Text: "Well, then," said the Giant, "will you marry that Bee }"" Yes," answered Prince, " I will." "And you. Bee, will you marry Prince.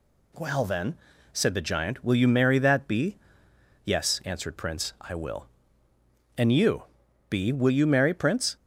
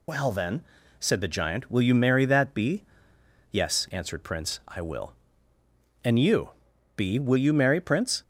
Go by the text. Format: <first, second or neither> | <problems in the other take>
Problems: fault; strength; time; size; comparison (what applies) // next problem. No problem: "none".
first | loses the start of "Well"; at 0.0 s; 70 ms